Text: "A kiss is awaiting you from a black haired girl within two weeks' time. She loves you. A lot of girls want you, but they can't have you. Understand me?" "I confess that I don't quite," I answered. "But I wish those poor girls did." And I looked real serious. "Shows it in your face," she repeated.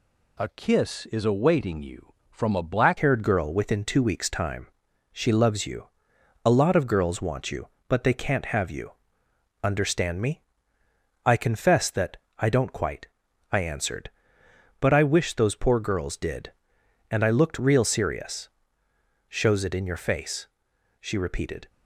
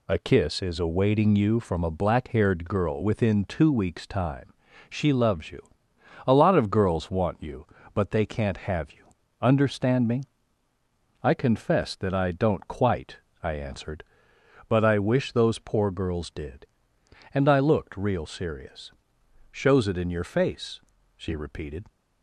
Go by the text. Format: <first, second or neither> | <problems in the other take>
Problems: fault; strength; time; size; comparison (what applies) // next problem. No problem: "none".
second | changes voice at "haired"; from 2.9 s on; 18.7 s long // pauses between "that" and "I"; slight; at 12.1 s; 0.20 s long